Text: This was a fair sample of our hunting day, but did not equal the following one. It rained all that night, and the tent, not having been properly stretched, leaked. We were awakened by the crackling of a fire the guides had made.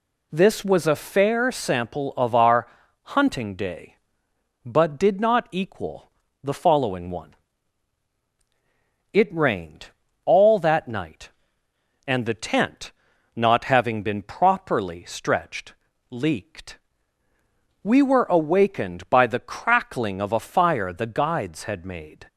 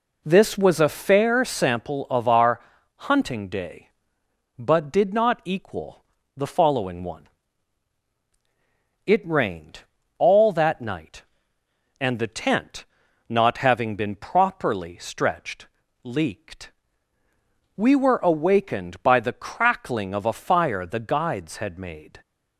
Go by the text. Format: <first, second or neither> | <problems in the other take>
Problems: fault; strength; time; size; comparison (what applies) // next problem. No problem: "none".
first | starts louder than the rest; until 1.9 s; 3.5 dB // pauses between "our" and "hunting"; slight; at 2.6 s; 0.36 s long; slight in the first // pauses between "equal" and "the"; slight; at 6.0 s; 0.32 s long; slight in the first // pauses between "rained" and "all"; at 9.8 s; 0.38 s long; also in the first